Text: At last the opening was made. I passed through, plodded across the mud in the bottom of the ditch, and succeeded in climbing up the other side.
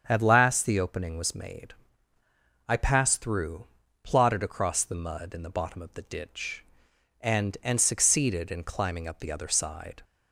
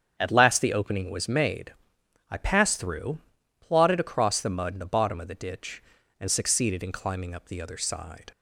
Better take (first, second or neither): second